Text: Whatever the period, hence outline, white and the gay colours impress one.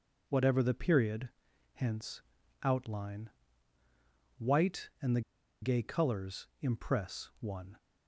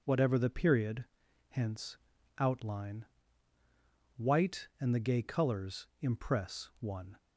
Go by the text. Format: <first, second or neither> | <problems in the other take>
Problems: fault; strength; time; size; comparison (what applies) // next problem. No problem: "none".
second | pauses between "hence" and "outline"; at 2.2 s; 0.44 s long; also in the second // pauses between "the" and "gay"; at 5.2 s; 0.41 s long